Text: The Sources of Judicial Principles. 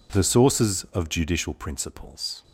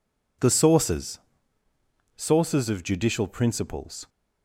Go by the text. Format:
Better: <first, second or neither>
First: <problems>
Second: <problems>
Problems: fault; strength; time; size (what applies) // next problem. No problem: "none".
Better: first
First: none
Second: says "Sources" twice; at 2.1 s